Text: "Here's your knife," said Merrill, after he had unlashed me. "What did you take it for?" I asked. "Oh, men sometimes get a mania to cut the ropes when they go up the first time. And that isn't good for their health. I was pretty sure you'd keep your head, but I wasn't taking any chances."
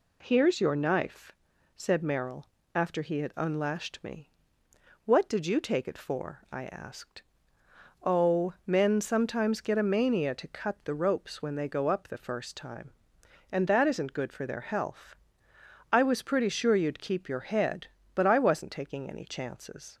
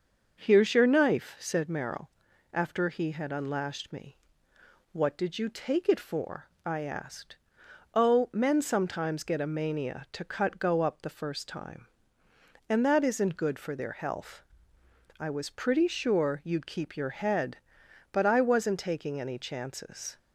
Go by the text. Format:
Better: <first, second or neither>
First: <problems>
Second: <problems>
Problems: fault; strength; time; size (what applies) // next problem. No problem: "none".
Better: first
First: none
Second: starts louder than the rest; until 1.4 s; 6.5 dB // skips "the ropes when they"; at 10.5 s